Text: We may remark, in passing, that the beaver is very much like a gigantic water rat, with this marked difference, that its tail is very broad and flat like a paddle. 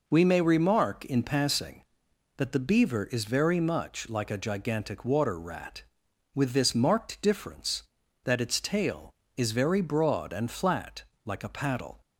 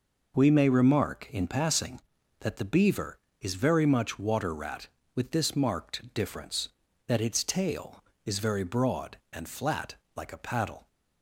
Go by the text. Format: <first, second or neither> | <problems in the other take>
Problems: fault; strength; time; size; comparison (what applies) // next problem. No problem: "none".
first | skips "like a gigantic"; at 4.1 s // pauses between "flat" and "like"; slight; at 9.9 s; 0.22 s long; slight in the first